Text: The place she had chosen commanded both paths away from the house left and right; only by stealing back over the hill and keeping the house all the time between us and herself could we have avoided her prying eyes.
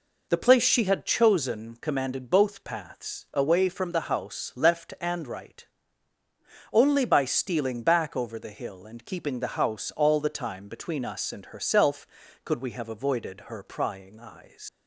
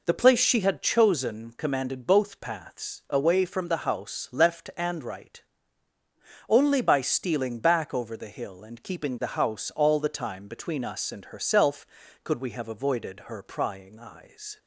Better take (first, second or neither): second